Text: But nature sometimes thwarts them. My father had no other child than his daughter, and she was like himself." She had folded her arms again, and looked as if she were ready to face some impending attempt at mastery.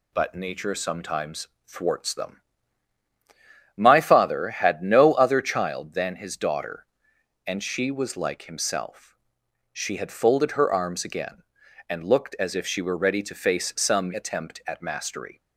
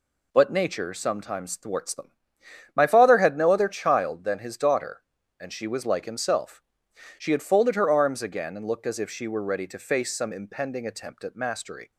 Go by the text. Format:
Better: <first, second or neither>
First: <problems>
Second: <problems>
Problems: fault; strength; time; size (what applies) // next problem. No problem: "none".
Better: second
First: pauses between "sometimes" and "thwarts"; slight; at 1.4 s; 0.18 s long // skips "impending"; at 14.1 s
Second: none